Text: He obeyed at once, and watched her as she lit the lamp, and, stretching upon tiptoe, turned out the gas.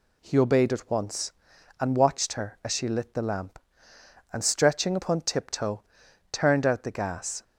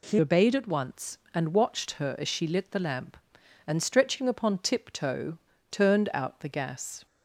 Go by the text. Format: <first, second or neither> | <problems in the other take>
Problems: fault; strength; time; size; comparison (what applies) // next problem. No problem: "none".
first | changes voice at "obeyed"; from 0.1 s on; 6.9 s long